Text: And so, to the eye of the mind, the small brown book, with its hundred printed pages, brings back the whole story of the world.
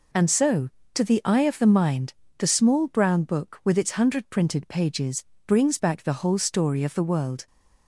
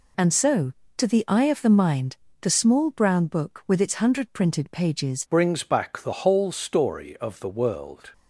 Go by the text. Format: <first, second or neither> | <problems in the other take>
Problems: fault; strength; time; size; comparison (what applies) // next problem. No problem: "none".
first | changes voice at "brings"; from 5.3 s on; 2.8 s long